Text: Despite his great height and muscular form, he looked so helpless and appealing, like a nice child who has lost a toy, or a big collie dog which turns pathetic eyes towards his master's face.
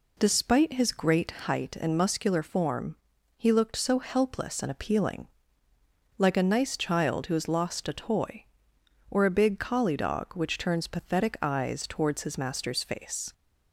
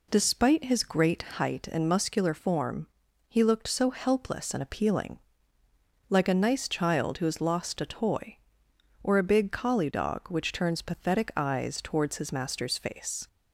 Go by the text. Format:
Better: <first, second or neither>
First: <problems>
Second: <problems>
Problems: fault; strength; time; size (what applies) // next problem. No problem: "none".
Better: neither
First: pauses between "great" and "height"; slight; at 1.2 s; 0.16 s long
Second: pauses between "great" and "height"; slight; at 1.2 s; 0.16 s long